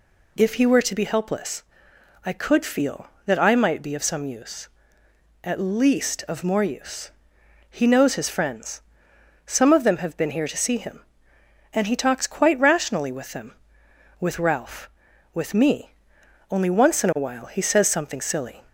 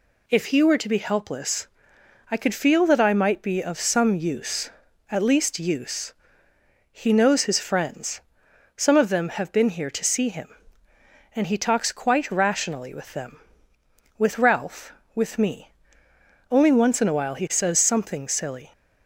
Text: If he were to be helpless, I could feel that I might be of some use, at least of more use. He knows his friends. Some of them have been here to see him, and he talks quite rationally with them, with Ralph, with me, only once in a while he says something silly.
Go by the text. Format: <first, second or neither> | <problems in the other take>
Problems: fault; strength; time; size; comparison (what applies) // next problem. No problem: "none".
first | skips "of more"; at 5.5 s